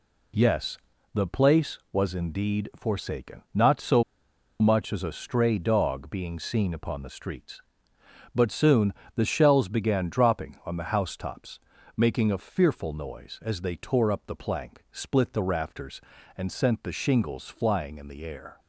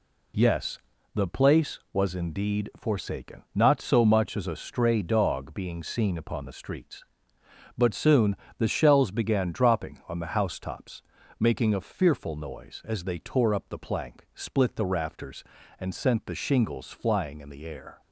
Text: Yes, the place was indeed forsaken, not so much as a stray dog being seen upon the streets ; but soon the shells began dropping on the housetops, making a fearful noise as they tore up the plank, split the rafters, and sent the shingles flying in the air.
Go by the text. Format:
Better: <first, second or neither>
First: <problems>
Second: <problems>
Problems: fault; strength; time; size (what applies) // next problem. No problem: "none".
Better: second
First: pauses between "so" and "much"; noticeable; at 4.0 s; 0.57 s long // pauses between "soon" and "the"; slight; at 8.9 s; 0.24 s long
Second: pauses between "soon" and "the"; slight; at 8.3 s; 0.24 s long